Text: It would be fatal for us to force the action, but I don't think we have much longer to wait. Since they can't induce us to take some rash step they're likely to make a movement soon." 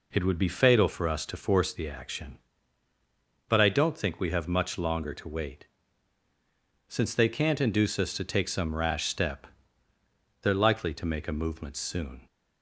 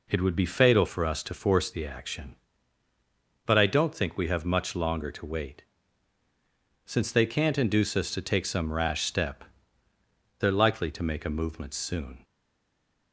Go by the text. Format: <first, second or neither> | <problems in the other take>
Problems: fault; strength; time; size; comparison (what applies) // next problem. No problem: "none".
first | pauses between "step" and "they're"; noticeable; at 9.4 s; 0.96 s long; noticeable in the first // stays silent after the last word; slight; from 12.2 s on; 0.9 s long